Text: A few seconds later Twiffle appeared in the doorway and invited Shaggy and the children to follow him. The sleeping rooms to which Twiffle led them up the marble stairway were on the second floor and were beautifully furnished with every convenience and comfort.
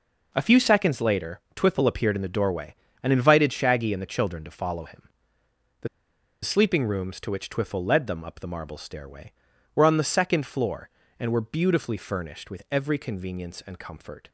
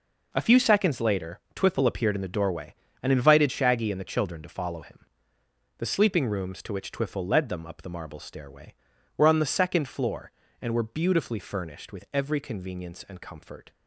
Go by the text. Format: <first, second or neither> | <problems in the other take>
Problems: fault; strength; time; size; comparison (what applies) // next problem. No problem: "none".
second | pauses between "later" and "Twiffle"; slight; at 1.3 s; 0.16 s long; slight in the second // pauses between "The" and "sleeping"; noticeable; at 5.8 s; 0.57 s long